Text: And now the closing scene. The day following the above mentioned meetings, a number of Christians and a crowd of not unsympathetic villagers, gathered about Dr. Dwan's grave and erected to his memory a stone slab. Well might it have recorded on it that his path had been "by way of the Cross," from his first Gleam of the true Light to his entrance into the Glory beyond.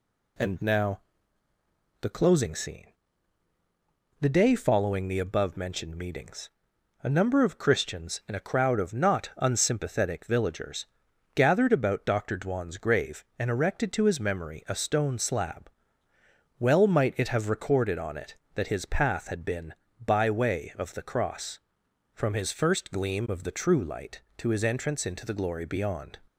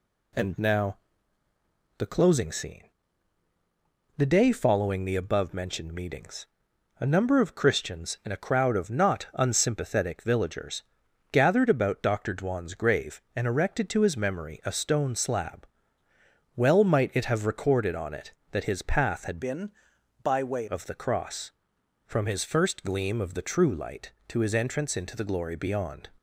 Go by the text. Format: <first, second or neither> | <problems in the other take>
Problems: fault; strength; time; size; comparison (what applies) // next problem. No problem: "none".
first | pauses between "now" and "the"; at 0.9 s; 1.0 s long; also in the first // changes voice from "been" to "way"; from 19.4 to 20.6 s; 1.2 s long